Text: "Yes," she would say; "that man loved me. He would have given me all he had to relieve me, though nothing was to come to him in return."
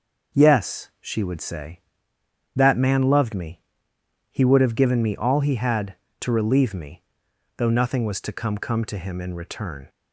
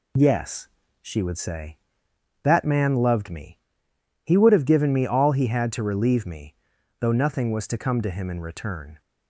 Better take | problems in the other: second | says "come" twice; at 8.5 s

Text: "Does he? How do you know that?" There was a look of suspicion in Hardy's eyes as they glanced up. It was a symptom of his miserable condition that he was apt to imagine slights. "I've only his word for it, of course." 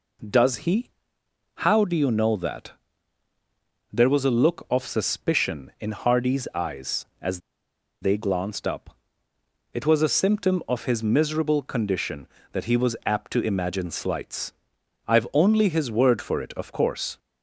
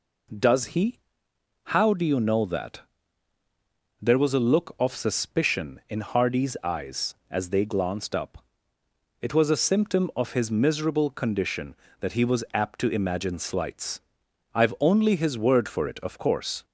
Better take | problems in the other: second | pauses between "as" and "they"; noticeable; at 7.3 s; 0.62 s long

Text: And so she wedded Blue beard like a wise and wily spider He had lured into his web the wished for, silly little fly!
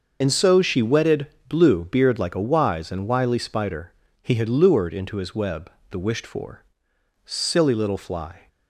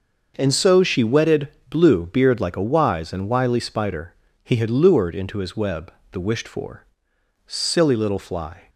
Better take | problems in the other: second | loses the start of "And"; at 0.2 s; 65 ms // starts louder than the rest; until 1.2 s; 6 dB; also in the second // pauses between "wedded" and "Blue"; slight; at 1.2 s; 0.20 s long; slight in the second // pauses between "spider" and "He"; slight; at 3.9 s; 0.30 s long; slight in the second // pauses between "web" and "the"; slight; at 5.7 s; 0.18 s long; slight in the second

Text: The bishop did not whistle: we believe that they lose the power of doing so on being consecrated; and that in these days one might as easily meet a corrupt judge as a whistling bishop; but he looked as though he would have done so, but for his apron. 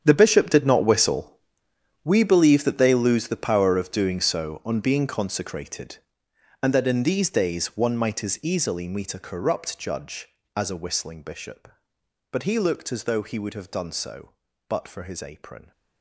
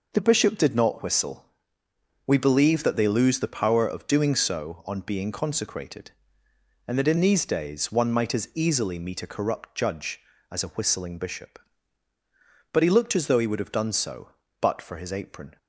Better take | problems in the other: second | gets quieter; strong; throughout; 15 dB

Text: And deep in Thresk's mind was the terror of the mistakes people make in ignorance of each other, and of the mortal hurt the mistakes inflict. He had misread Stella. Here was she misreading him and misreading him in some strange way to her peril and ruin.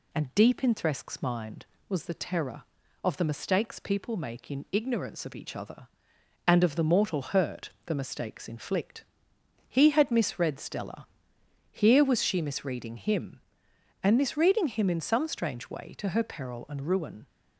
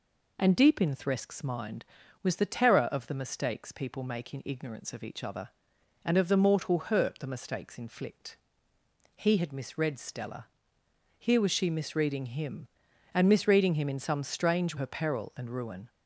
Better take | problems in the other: first | skips "way to"; at 14.7 s

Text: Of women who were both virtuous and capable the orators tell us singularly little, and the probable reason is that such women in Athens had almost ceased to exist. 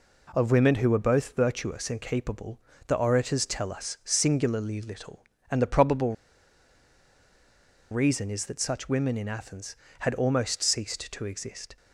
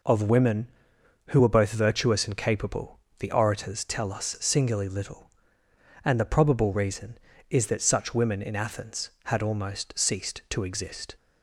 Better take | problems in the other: second | pauses between "capable" and "the"; slight; at 2.6 s; 0.26 s long; slight in the second // pauses between "probable" and "reason"; strong; at 6.1 s; 1.7 s long

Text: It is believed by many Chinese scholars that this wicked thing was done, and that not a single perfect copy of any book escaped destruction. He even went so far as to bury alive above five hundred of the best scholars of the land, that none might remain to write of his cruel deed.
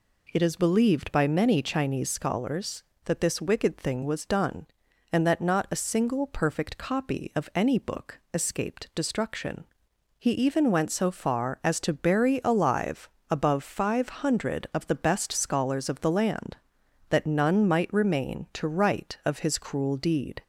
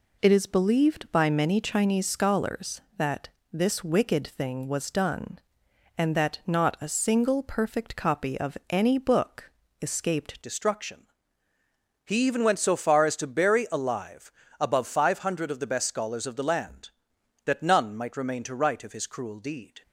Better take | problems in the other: first | pauses between "that" and "this"; slight; at 3.2 s; 0.24 s long // pauses between "book" and "escaped"; slight; at 9.5 s; 0.30 s long // changes voice at "destruction"; from 10.4 s on; 9.4 s long // pauses between "alive" and "above"; slight; at 14.3 s; 0.28 s long; slight in the first

